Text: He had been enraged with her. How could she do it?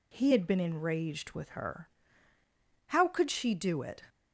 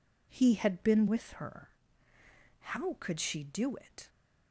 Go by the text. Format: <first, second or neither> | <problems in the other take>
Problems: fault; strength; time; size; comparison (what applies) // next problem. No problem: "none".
first | skips "enraged"; at 1.0 s